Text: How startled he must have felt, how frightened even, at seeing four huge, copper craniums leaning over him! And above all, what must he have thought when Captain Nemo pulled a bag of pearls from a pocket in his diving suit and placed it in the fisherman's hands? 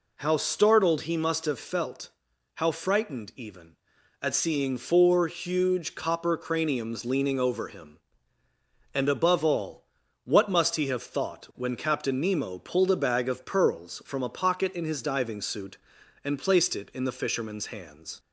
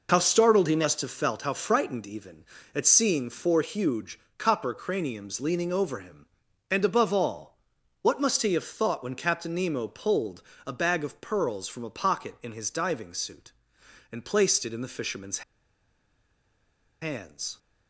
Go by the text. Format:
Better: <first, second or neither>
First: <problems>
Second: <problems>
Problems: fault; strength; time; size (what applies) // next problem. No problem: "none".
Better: first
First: none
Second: pauses between "pulled" and "a"; slight; at 10.4 s; 0.24 s long // pauses between "fisherman's" and "hands"; strong; at 15.4 s; 1.6 s long